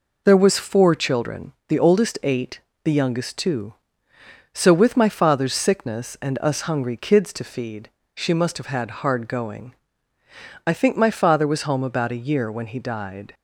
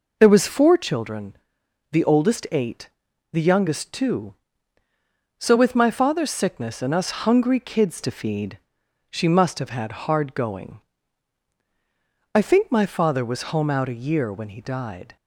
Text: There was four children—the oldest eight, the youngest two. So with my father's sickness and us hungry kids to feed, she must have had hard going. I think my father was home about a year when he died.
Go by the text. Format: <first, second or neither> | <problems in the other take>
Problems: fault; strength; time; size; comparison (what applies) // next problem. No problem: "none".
first | says "out" for "about"; at 13.7 s